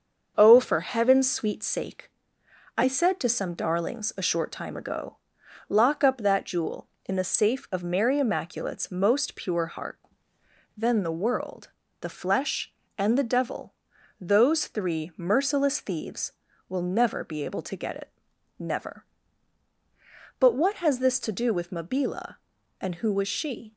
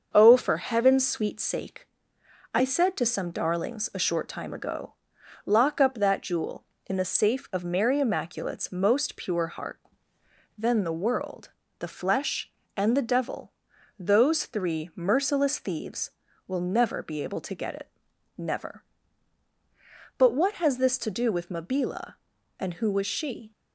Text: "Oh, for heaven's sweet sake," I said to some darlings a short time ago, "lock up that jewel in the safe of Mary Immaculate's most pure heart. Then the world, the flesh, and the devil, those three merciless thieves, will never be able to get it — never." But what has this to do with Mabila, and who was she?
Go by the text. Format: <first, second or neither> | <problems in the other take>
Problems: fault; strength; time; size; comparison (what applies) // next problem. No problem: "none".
neither | starts louder than the rest; the same in both